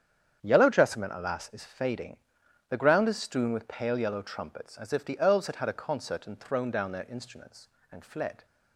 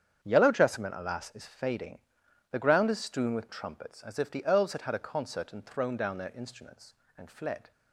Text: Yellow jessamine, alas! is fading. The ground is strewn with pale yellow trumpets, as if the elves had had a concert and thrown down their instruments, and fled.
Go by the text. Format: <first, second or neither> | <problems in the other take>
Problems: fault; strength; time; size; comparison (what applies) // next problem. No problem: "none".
first | starts louder than the rest; strong; until 1.2 s; 8 dB; strong in the first // skips "pale yellow"; at 3.4 s